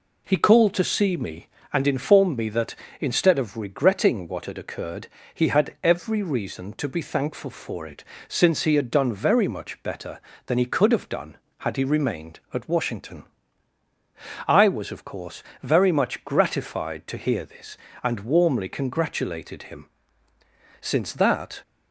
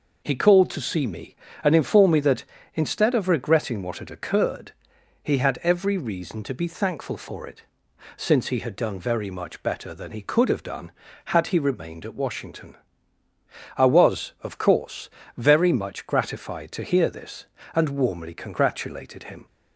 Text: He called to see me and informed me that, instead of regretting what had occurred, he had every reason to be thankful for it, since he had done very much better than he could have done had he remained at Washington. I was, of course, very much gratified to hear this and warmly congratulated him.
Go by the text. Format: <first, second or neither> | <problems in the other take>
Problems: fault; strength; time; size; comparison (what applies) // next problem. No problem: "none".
second | goes on to say "Since that"; noticeable; from 20.8 s on; 0.80 s long